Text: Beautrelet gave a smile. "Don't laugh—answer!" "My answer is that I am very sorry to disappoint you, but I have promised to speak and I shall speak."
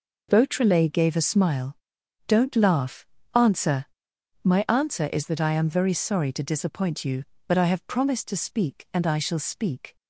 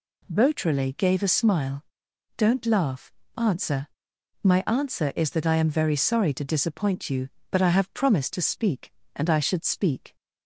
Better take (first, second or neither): first